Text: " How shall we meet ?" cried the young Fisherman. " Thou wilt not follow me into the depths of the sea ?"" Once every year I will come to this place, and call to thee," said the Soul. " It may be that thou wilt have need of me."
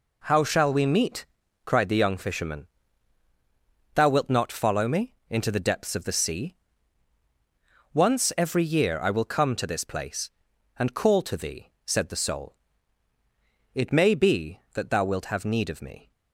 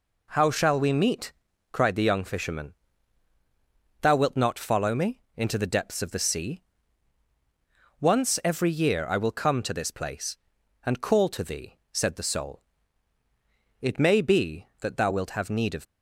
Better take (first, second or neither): first